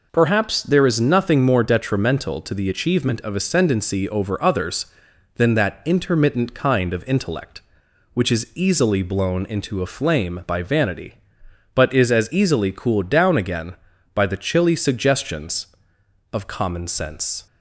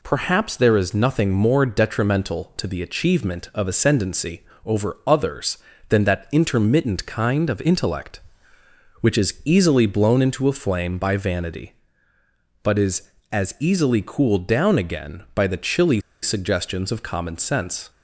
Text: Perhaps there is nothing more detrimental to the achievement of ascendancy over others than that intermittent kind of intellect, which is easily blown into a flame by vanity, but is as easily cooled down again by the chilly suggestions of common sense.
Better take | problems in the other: first | pauses between "ascendancy" and "over"; slight; at 4.4 s; 0.22 s long // pauses between "chilly" and "suggestions"; slight; at 16.0 s; 0.21 s long

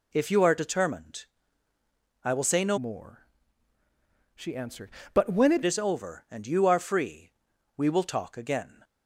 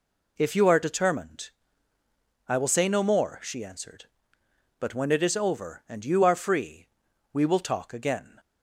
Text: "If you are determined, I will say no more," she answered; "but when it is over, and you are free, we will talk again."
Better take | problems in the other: second | changes voice from "more" to "it"; from 2.7 to 5.6 s; 2.9 s long

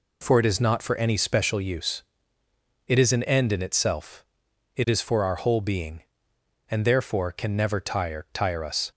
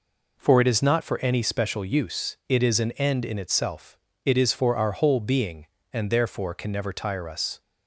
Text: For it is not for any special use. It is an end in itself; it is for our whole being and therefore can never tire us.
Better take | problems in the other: second | says "tire" twice; at 8.3 s

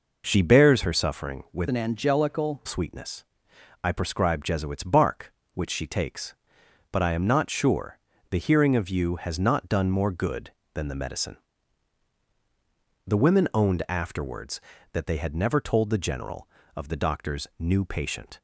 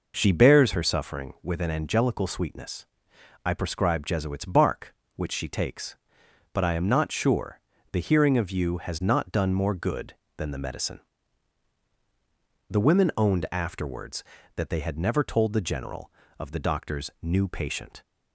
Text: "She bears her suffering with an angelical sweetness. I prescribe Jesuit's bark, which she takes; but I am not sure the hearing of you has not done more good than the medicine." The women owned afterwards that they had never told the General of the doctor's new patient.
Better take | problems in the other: second | changes voice from "an" to "angelical"; from 1.6 to 2.6 s; 1.0 s long // pauses between "sure" and "the"; slight; at 7.9 s; 0.32 s long; slight in the second

